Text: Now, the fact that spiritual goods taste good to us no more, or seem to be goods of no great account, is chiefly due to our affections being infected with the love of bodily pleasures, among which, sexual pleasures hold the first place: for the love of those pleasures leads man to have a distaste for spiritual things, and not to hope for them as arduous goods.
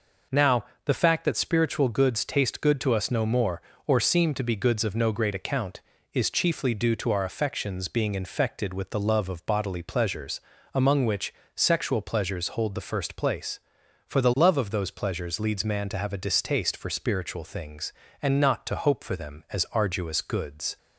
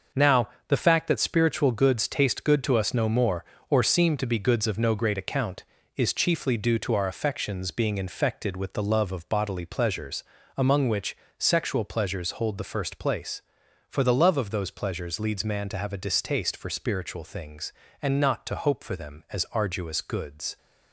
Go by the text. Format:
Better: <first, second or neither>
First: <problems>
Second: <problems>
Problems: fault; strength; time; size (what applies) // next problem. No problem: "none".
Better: first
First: none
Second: gets quieter; strong; throughout; 8 dB